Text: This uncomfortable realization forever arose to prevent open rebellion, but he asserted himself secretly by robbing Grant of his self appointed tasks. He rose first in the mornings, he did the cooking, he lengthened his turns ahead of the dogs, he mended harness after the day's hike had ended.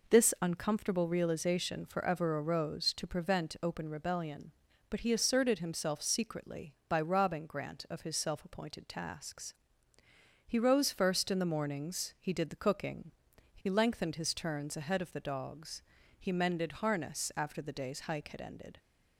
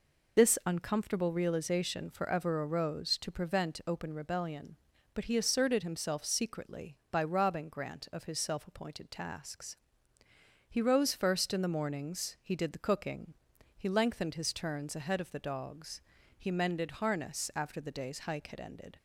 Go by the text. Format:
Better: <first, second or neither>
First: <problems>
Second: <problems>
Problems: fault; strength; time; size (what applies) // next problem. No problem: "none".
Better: first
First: none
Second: loses the start of "This"; at 0.3 s; 70 ms